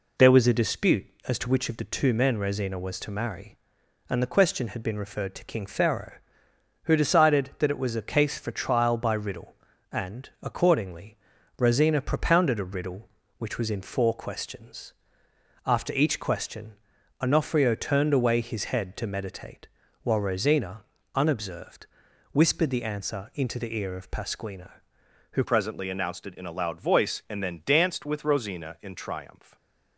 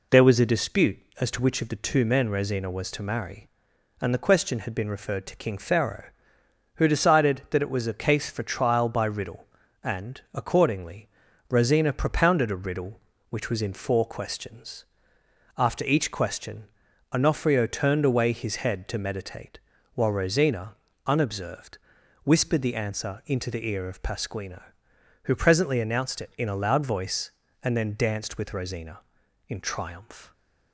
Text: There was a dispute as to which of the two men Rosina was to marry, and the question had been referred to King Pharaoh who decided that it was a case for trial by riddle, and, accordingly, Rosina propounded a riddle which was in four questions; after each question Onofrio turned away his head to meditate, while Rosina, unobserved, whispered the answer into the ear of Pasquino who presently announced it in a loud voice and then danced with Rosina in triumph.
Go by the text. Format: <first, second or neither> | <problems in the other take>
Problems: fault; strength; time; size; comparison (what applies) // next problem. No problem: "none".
second | pauses between "question" and "Onofrio"; at 16.7 s; 0.44 s long; also in the second // changes voice at "presently"; from 25.4 s on; 4.1 s long // stays silent after the last word; slight; from 29.4 s on; 0.5 s long